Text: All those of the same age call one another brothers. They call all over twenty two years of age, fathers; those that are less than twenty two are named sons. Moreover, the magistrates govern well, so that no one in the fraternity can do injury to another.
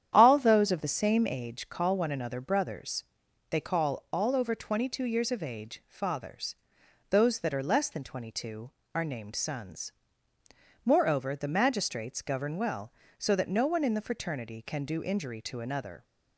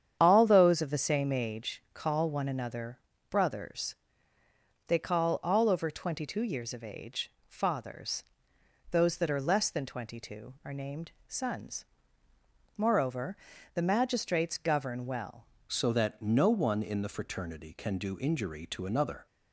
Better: first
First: starts louder than the rest; strong; until 1.1 s; 9.5 dB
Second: starts louder than the rest; strong; until 1.2 s; 8.5 dB // pauses between "another" and "brothers"; slight; at 2.9 s; 0.34 s long // pauses between "named" and "sons"; slight; at 11.0 s; 0.18 s long // changes voice at "so"; from 15.6 s on; 3.6 s long

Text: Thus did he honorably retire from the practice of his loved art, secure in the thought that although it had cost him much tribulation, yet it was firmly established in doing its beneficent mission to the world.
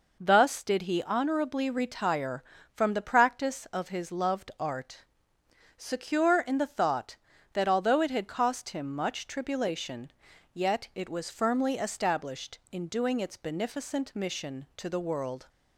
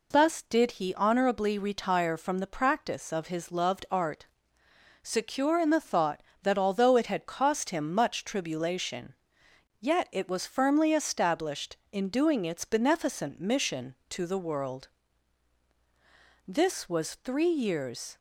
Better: first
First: none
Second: goes on to say "This was three years"; strong; from 16.4 s on; 1.6 s long

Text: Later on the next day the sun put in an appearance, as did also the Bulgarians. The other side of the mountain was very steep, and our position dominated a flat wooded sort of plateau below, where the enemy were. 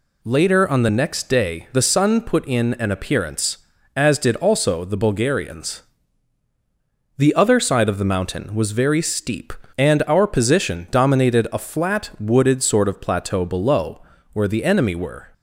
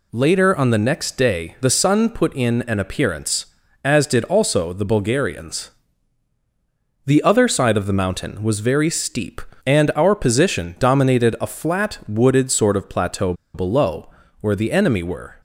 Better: first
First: none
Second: pauses between "plateau" and "below"; slight; at 13.3 s; 0.20 s long

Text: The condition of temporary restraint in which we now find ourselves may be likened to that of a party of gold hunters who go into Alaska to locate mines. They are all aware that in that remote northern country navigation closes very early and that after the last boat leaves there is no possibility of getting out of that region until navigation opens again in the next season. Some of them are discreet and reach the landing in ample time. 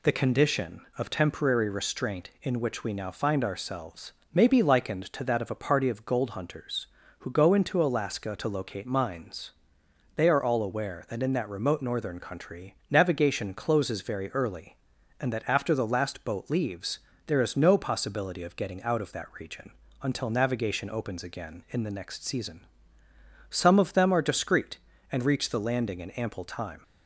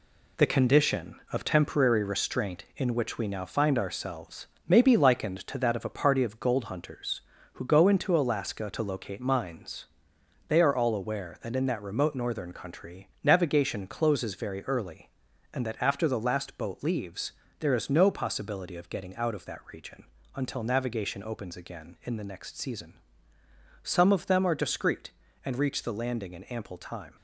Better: first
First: pauses between "ourselves" and "may"; slight; at 4.1 s; 0.20 s long // pauses between "leaves" and "there"; slight; at 17.0 s; 0.26 s long // pauses between "region" and "until"; slight; at 19.7 s; 0.28 s long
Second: gets quieter; throughout; 6.5 dB // pauses between "ourselves" and "may"; slight; at 4.4 s; 0.20 s long // pauses between "leaves" and "there"; slight; at 17.3 s; 0.26 s long // pauses between "region" and "until"; slight; at 20.0 s; 0.28 s long

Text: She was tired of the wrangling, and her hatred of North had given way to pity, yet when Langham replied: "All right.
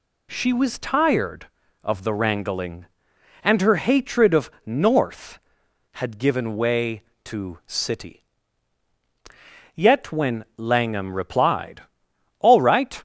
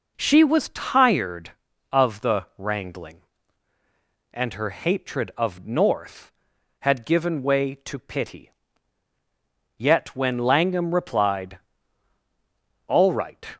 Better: second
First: says "city" for "pity"; at 7.6 s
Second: none

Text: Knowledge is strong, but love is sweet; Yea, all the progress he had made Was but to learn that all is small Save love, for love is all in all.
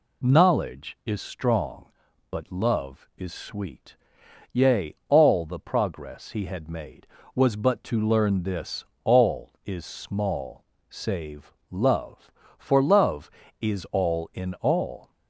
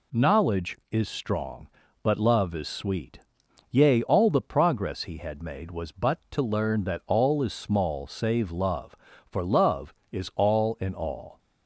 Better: second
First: says "this" for "that"; at 8.4 s // pauses between "small" and "Save"; slight; at 10.6 s; 0.24 s long // pauses between "Save" and "love"; slight; at 11.5 s; 0.20 s long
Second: none

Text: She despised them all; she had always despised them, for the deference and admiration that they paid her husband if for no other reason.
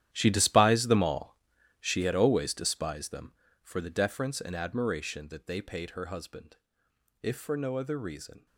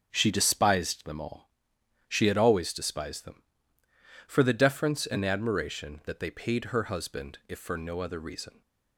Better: second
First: gets quieter; strong; throughout; 15 dB // starts louder than the rest; strong; until 1.1 s; 11.5 dB // pauses between "husband" and "if"; noticeable; at 6.5 s; 0.64 s long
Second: starts louder than the rest; until 1.1 s; 6.5 dB

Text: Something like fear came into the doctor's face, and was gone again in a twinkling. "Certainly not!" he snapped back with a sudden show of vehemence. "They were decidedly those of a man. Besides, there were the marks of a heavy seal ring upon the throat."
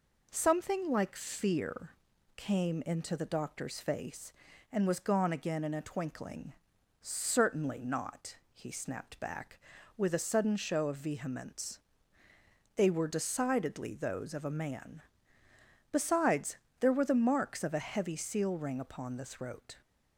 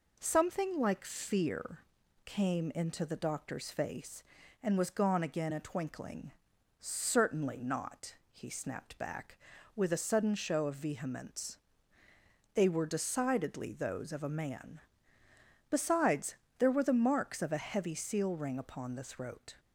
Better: first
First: pauses between "fear" and "came"; at 1.9 s; 0.42 s long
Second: pauses between "fear" and "came"; at 1.8 s; 0.42 s long // skips "in"; at 5.5 s

